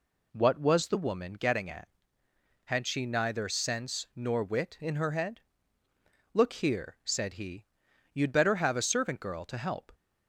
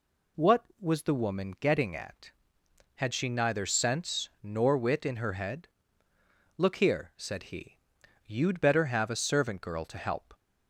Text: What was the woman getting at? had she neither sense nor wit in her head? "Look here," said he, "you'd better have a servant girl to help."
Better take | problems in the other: neither | none

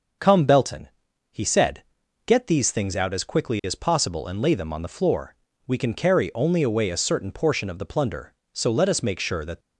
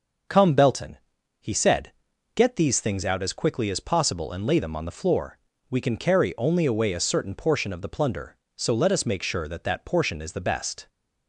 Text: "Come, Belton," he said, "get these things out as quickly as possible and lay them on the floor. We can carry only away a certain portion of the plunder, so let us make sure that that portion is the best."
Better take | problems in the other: second | starts louder than the rest; until 1.6 s; 6.5 dB; also in the second // stops before "that portion is the best"; at 9.5 s

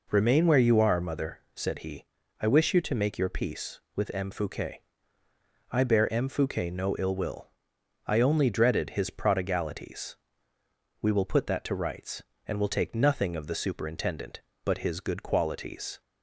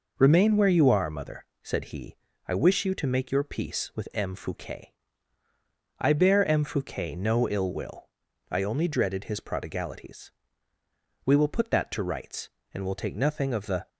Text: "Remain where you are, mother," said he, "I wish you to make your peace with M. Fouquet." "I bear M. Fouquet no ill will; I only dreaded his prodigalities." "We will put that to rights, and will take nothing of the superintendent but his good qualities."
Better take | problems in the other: first | stops before "superintendent but his good qualities"; at 13.8 s

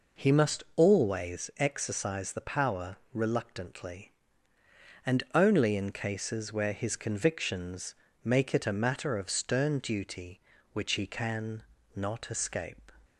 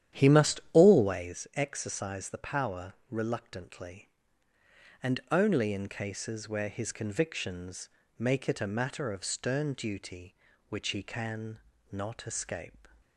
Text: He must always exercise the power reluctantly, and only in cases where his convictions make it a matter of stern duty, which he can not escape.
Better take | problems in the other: first | starts louder than the rest; strong; until 1.3 s; 10.5 dB // pauses between "power" and "reluctantly"; slight; at 2.9 s; 0.16 s long; slight in the first // pauses between "convictions" and "make"; slight; at 7.8 s; 0.32 s long; slight in the first // pauses between "can" and "not"; slight; at 11.5 s; 0.34 s long; slight in the first

